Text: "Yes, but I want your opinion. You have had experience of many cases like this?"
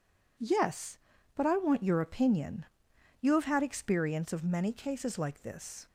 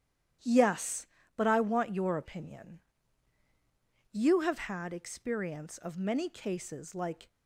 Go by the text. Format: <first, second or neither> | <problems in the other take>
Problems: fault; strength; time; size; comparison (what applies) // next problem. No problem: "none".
first | starts louder than the rest; strong; until 1.6 s; 10.5 dB // stops before "this"; at 7.2 s